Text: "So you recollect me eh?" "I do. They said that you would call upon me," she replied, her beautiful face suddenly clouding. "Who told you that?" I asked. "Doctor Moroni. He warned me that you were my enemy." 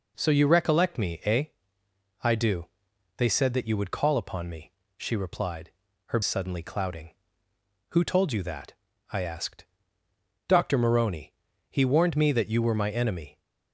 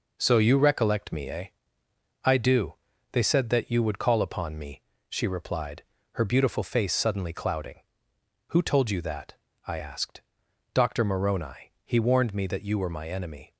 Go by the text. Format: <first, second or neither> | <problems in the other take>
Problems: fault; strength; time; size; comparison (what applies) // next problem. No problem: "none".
second | skips "beautiful face"; at 6.2 s